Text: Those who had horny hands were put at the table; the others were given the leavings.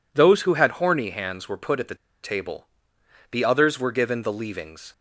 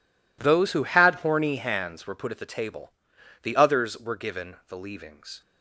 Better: second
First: pauses between "the" and "table"; slight; at 1.9 s; 0.28 s long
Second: none

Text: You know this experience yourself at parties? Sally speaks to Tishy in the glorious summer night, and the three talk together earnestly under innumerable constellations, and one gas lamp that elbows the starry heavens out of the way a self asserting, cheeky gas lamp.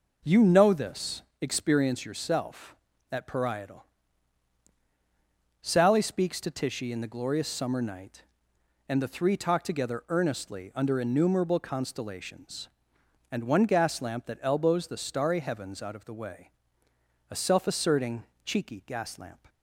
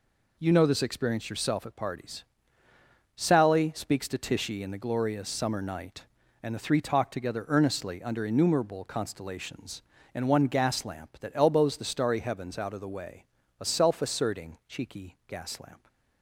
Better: second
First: pauses between "this" and "experience"; slight; at 1.2 s; 0.18 s long // says "parietal" for "parties"; at 3.2 s // pauses between "way" and "a"; noticeable; at 16.5 s; 0.78 s long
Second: pauses between "way" and "a"; slight; at 13.2 s; 0.36 s long

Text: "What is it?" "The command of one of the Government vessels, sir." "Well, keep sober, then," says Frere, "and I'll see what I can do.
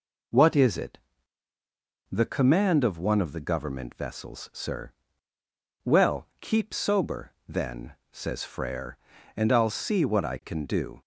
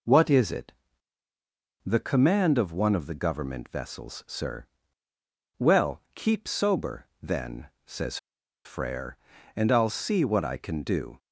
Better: first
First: none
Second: pauses between "says" and "Frere"; noticeable; at 8.1 s; 0.48 s long

